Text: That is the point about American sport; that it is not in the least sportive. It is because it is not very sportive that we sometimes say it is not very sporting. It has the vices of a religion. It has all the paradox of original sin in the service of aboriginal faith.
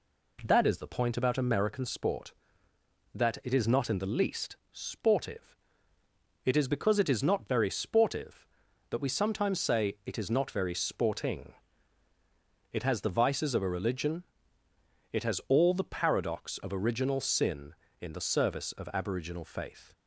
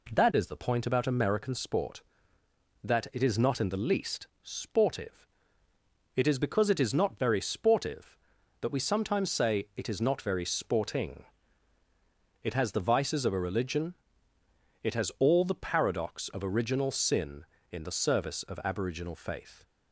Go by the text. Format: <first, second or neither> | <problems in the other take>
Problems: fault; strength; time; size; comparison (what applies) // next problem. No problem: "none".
neither | pauses between "least" and "sportive"; slight; the same in both